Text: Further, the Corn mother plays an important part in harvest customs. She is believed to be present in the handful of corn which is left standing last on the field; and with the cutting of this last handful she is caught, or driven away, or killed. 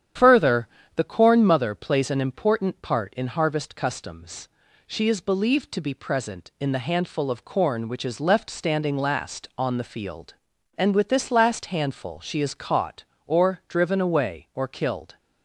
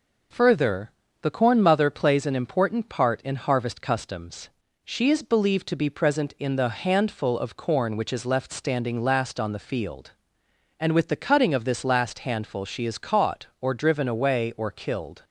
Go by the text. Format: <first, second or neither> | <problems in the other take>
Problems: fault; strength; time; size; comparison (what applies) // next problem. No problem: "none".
second | starts louder than the rest; strong; until 1.4 s; 9.5 dB // skips "the cutting of"; at 11.0 s